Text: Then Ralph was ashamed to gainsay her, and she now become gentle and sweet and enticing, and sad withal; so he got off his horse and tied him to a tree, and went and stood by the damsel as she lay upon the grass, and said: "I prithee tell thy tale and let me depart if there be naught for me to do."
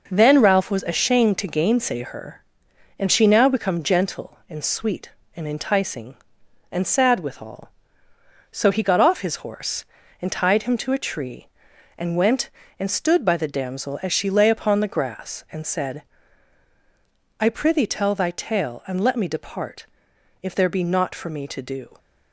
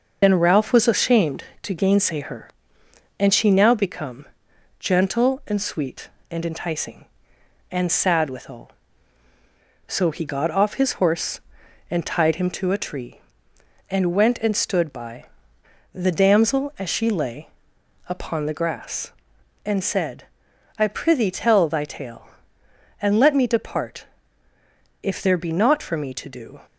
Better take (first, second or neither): first